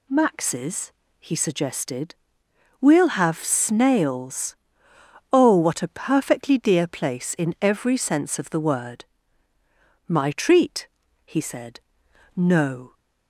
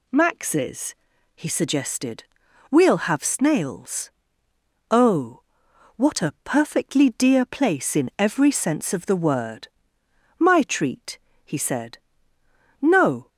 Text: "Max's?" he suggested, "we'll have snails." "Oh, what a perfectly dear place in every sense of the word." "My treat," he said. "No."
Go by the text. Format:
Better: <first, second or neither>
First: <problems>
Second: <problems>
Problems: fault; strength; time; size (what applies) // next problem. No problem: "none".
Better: neither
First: none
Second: none